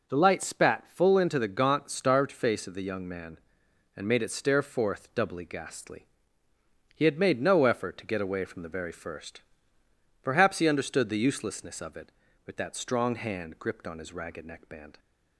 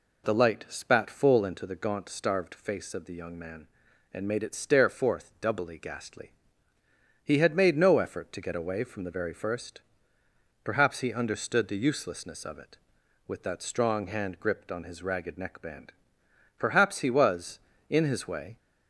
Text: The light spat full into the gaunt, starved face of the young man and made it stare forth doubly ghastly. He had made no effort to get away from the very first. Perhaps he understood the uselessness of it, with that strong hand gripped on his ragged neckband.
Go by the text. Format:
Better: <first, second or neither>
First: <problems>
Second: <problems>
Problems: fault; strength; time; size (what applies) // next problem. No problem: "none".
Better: first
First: none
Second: goes on to say "Perhaps he was in his way"; strong; from 16.5 s on; 1.9 s long